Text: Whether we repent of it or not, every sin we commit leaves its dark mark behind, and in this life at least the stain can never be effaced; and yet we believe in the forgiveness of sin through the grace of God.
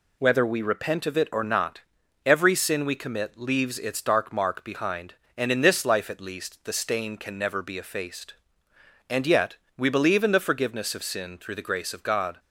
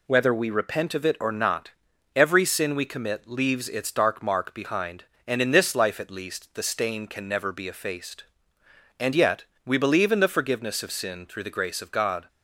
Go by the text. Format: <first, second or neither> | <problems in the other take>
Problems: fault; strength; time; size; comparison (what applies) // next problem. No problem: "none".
neither | pauses between "yet" and "we"; slight; the same in both